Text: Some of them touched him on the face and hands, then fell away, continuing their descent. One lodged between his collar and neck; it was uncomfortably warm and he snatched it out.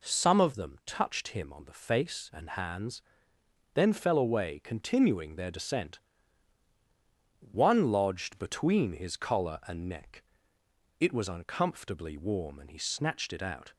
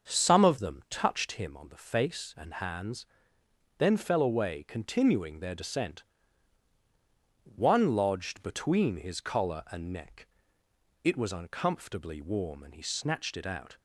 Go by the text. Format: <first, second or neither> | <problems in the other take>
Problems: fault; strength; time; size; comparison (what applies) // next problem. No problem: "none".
first | starts louder than the rest; until 1.4 s; 6.5 dB